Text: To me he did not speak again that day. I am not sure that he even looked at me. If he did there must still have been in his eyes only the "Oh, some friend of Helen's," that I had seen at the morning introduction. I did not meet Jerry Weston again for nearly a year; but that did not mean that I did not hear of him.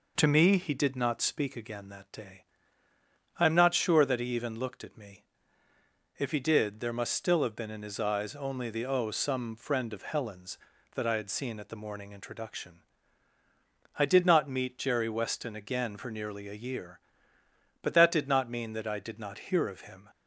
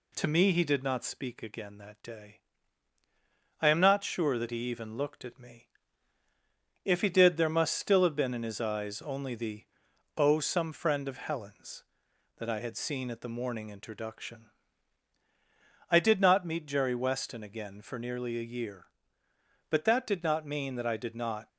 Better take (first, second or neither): first